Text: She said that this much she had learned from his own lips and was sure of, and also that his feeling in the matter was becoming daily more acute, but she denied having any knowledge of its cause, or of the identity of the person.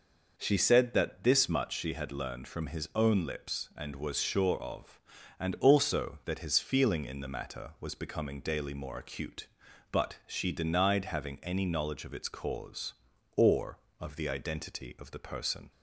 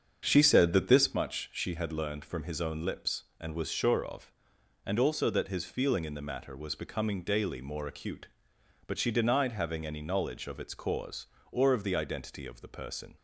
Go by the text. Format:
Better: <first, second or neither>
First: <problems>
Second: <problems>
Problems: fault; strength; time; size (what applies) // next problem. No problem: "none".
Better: first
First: none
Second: starts louder than the rest; strong; until 1.2 s; 7 dB